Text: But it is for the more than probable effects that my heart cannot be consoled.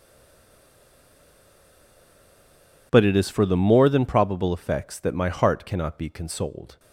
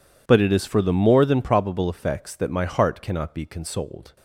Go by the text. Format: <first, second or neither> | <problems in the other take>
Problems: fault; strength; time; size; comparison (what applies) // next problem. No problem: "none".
second | stays silent before the first word; strong; until 2.9 s; 2.9 s long